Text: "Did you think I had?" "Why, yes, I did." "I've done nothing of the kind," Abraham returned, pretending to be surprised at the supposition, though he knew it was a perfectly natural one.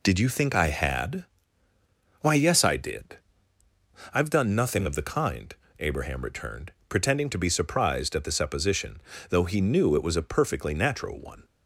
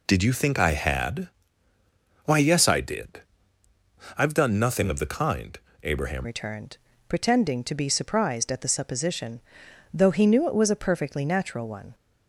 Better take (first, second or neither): first